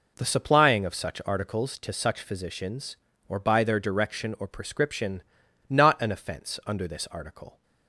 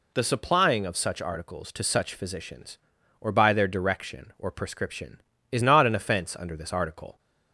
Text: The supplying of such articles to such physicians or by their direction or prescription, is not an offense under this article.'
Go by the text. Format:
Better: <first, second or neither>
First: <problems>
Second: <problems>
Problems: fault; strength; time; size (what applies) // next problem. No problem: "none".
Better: second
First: skips "is"; at 5.4 s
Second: none